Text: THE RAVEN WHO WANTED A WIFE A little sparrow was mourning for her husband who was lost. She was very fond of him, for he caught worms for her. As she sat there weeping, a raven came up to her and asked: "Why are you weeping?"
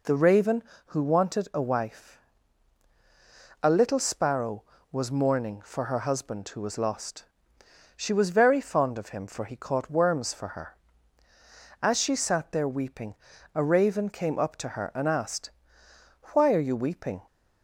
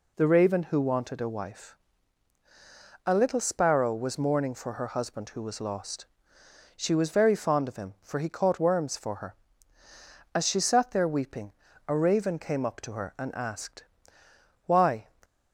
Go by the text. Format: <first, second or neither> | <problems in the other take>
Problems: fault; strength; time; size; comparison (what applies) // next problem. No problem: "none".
first | pauses between "WIFE" and "A"; strong; at 1.7 s; 1.3 s long; strong in the first // stops before "are you weeping"; at 15.2 s